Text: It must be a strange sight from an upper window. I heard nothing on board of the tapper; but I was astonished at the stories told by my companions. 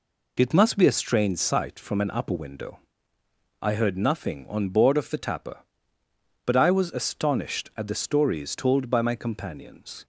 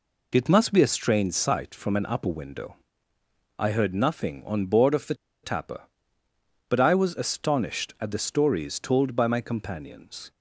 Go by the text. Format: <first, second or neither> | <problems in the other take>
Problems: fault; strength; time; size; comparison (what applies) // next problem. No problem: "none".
first | pauses between "the" and "tapper"; slight; at 5.1 s; 0.29 s long